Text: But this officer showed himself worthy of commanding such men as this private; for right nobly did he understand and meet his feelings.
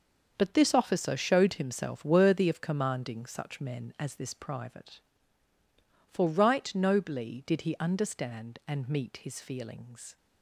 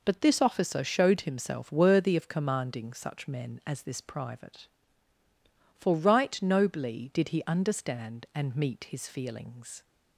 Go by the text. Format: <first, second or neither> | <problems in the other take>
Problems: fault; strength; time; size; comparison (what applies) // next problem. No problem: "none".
second | gets quieter; strong; throughout; 10 dB